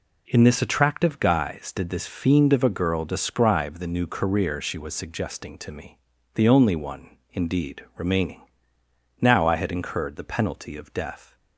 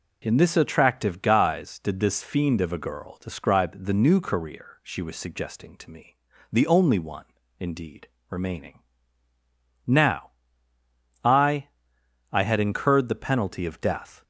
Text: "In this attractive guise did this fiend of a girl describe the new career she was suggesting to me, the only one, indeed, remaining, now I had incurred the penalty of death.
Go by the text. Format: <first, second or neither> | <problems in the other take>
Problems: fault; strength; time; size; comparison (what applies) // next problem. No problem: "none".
first | pauses between "now" and "I"; noticeable; at 10.3 s; 0.94 s long // says "I" twice; at 12.3 s